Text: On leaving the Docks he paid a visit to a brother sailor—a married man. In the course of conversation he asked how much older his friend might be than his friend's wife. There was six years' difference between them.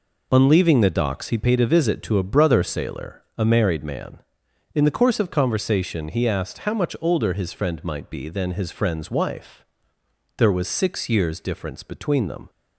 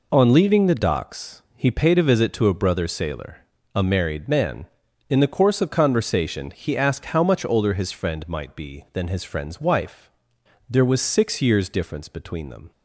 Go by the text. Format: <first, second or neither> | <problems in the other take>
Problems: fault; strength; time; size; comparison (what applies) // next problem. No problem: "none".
neither | none